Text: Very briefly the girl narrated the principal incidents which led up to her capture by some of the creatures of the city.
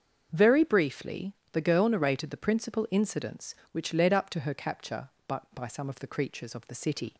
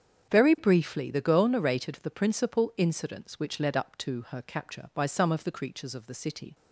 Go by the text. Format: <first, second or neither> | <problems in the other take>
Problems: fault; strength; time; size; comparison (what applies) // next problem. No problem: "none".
second | starts louder than the rest; until 1.3 s; 7 dB; strong in the second // pauses between "briefly" and "the"; slight; at 1.3 s; 0.18 s long // says "by" twice; at 5.5 s